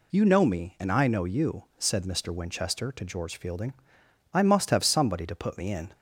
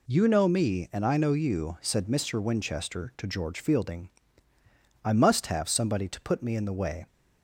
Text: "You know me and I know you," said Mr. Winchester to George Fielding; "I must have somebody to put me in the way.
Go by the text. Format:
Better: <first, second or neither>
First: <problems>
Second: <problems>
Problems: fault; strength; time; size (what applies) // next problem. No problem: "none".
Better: second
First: stops before "the way"; at 5.9 s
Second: none